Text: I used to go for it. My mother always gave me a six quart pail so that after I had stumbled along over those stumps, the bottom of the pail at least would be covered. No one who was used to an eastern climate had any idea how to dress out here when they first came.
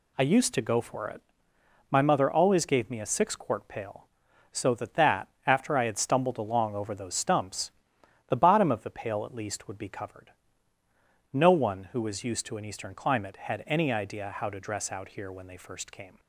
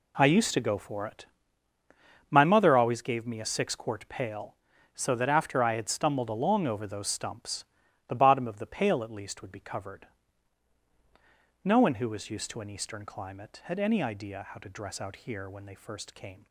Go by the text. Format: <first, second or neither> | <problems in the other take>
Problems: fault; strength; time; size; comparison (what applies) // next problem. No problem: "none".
second | says "that" twice; at 4.9 s